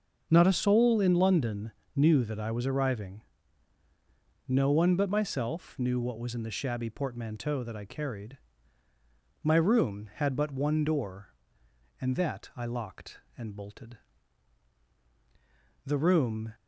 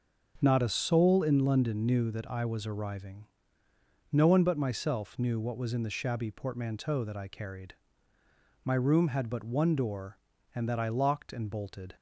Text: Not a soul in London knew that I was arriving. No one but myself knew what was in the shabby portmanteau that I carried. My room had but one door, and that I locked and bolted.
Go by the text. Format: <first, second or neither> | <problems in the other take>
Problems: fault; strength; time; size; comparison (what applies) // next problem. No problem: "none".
second | starts louder than the rest; until 1.3 s; 6.5 dB; also in the second // pauses between "London" and "knew"; slight; at 1.7 s; 0.24 s long // goes on to say "The room"; noticeable; from 15.8 s on; 0.68 s long